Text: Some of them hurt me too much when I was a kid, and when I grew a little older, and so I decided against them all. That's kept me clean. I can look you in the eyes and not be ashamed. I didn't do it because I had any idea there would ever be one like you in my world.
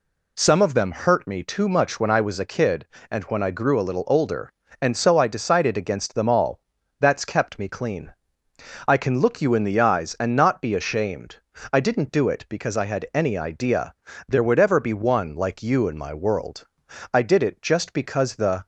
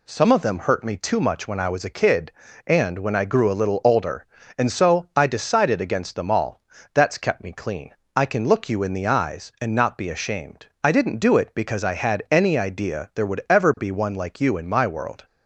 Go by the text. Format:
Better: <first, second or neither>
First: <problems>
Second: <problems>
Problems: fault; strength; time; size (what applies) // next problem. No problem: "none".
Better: second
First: pauses between "idea" and "there"; slight; at 13.9 s; 0.33 s long // goes on to say "I did it just because the"; from 17.1 s on; 1.5 s long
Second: none